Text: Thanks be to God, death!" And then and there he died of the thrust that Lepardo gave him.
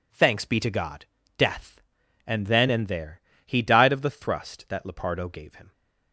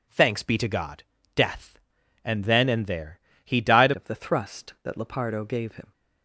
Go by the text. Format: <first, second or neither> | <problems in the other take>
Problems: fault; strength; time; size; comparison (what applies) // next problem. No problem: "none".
first | pauses between "there" and "he"; slight; at 3.1 s; 0.24 s long; slight in the first // changes voice at "of"; from 3.9 s on; 2.0 s long